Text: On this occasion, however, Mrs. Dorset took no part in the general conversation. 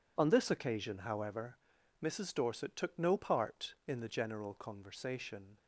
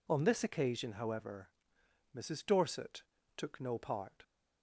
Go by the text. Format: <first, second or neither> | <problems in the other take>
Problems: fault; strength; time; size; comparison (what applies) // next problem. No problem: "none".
first | pauses between "Dorset" and "took"; slight; at 3.0 s; 0.32 s long // stops before "in the general conversation"; at 4.2 s